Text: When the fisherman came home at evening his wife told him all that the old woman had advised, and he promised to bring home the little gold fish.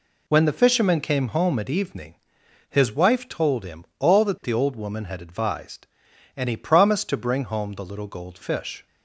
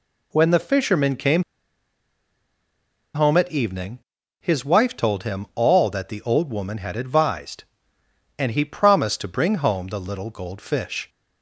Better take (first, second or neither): first